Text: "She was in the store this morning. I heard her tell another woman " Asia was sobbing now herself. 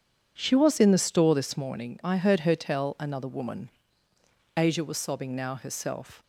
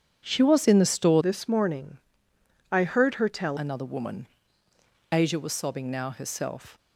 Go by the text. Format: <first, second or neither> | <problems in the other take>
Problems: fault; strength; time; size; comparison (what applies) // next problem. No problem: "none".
first | starts louder than the rest; strong; until 1.2 s; 9 dB; strong in the first // changes voice from "this" to "tell"; from 1.2 to 3.5 s; 2.3 s long